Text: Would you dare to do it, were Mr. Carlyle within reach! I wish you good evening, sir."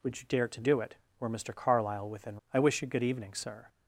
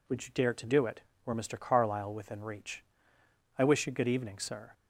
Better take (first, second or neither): second